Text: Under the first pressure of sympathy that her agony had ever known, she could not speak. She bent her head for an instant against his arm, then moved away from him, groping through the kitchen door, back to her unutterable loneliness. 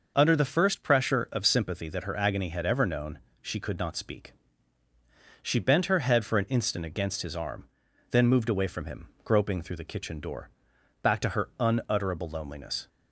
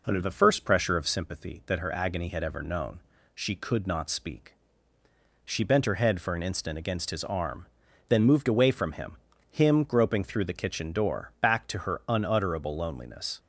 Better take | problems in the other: first | says "him" twice; at 9.4 s

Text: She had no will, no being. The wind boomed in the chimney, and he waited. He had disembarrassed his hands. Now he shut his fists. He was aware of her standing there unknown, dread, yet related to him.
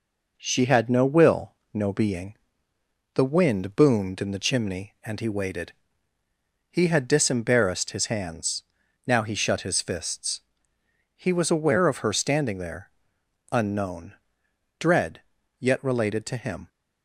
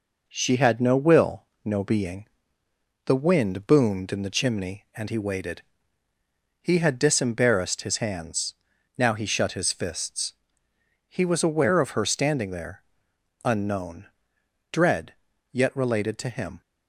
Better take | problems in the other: neither | pauses between "there" and "unknown"; noticeable; the same in both

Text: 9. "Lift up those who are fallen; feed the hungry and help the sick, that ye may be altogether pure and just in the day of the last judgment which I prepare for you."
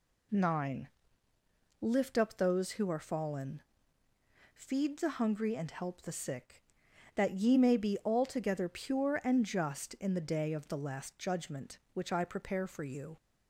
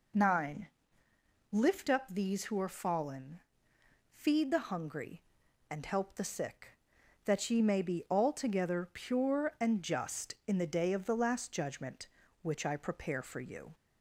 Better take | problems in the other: first | says "these" for "those"; at 2.0 s

